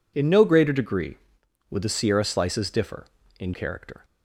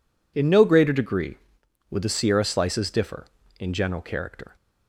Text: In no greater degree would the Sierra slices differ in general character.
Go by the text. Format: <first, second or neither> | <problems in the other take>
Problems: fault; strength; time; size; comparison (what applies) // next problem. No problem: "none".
second | skips "general"; at 3.5 s